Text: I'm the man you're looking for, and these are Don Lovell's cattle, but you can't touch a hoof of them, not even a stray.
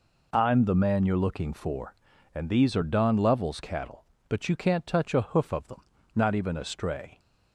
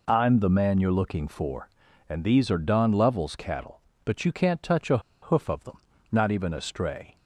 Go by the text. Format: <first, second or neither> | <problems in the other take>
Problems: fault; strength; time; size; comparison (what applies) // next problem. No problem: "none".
first | pauses between "a" and "hoof"; slight; at 4.9 s; 0.23 s long